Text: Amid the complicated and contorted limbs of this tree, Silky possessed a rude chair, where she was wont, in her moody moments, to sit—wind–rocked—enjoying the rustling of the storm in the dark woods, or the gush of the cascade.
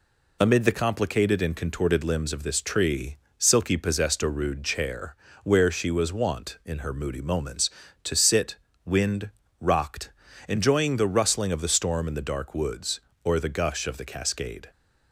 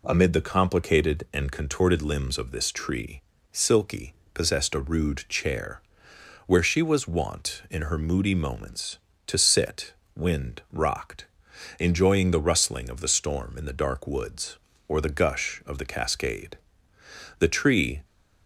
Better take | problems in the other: first | pauses between "Silky" and "possessed"; slight; at 4.1 s; 0.22 s long // goes on to say "The tree"; noticeable; from 17.3 s on; 0.64 s long

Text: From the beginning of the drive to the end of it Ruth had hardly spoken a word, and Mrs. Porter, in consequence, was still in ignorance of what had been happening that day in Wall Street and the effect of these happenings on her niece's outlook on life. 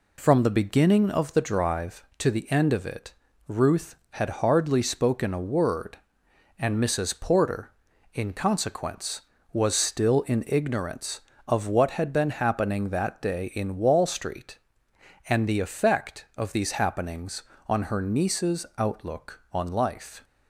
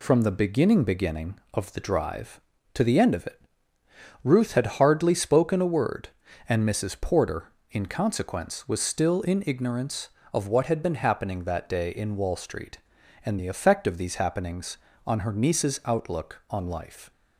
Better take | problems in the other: first | says "beginning" twice; at 0.8 s // pauses between "it" and "Ruth"; noticeable; at 3.3 s; 0.84 s long; slight in the first

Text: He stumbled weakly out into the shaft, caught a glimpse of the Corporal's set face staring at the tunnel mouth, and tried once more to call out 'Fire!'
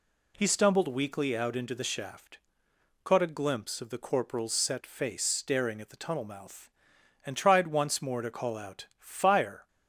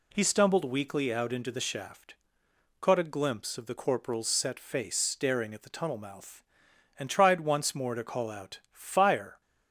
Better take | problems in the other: neither | none

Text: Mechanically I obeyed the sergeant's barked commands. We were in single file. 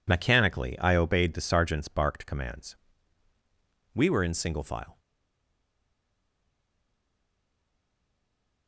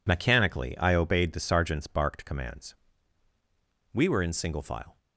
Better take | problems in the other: second | stays silent after the last word; strong; from 4.9 s on; 3.7 s long

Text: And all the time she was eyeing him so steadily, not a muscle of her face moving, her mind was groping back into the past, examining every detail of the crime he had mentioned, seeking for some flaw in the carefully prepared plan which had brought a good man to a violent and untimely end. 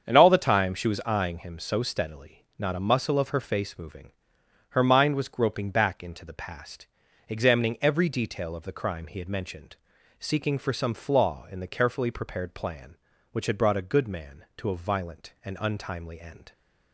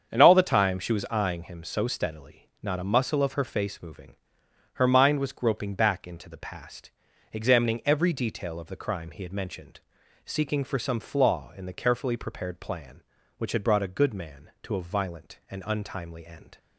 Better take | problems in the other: neither | starts louder than the rest; strong; the same in both

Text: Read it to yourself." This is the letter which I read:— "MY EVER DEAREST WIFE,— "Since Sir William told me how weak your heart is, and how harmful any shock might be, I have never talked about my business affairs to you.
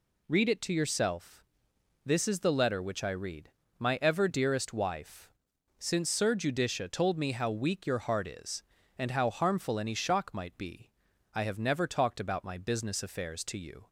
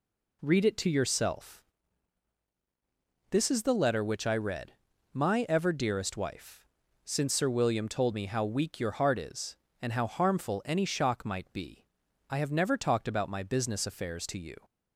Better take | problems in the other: second | says "Judicia" for "William"; at 6.3 s

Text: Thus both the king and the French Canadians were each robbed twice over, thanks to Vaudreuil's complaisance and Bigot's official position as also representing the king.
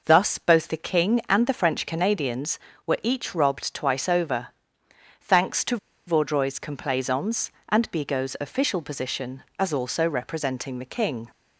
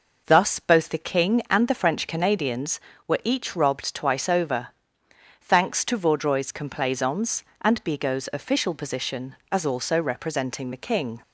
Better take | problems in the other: second | pauses between "to" and "Vaudreuil's"; slight; at 5.7 s; 0.30 s long

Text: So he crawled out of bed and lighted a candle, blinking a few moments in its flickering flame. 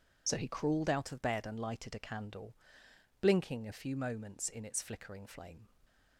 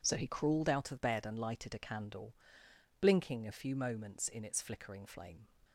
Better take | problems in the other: second | loses the start of "So"; at 0.2 s; 35 ms

